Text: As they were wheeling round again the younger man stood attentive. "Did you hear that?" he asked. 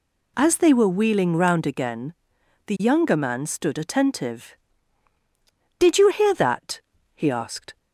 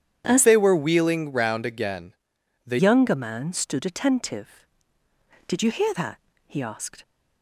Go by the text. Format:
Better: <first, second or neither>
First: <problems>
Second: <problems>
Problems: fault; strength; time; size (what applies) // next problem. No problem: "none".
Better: first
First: pauses between "again" and "the"; noticeable; at 2.1 s; 0.52 s long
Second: starts louder than the rest; strong; until 1.2 s; 9 dB // changes voice from "they" to "the"; from 0.4 to 2.7 s; 2.3 s long // pauses between "again" and "the"; noticeable; at 2.1 s; 0.54 s long